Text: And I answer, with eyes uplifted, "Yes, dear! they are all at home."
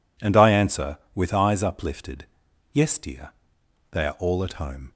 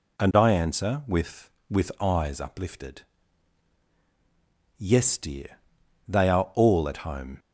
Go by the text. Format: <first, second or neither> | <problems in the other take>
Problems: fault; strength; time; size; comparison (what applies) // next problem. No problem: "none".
first | says "with" twice; at 1.6 s